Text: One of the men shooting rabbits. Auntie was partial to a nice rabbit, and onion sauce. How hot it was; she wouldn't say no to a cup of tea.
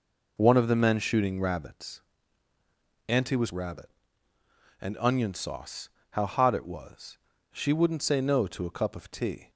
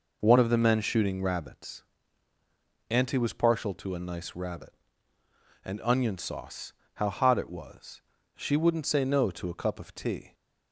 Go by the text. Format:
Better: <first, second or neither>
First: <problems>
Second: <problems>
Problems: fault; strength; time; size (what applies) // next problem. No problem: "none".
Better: second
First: skips "partial to a nice"; at 3.5 s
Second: none